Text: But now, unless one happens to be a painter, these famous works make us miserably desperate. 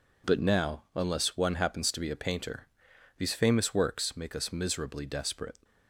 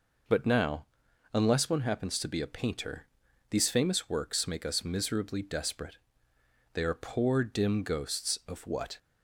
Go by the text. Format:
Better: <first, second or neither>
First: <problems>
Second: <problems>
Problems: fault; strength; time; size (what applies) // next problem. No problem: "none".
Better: first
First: none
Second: goes on to say "They are poor dim ghosts of what"; strong; from 6.7 s on; 2.2 s long